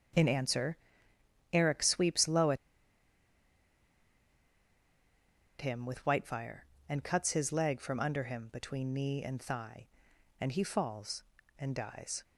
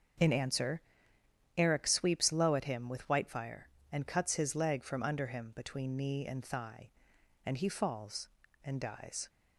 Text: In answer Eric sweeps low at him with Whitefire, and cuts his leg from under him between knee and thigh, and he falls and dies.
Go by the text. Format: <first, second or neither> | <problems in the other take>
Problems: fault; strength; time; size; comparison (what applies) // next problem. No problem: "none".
second | starts louder than the rest; strong; until 1.9 s; 7.5 dB; strong in the second // pauses between "answer" and "Eric"; noticeable; at 0.7 s; 0.76 s long; noticeable in the second // pauses between "at" and "him"; strong; at 2.5 s; 3.0 s long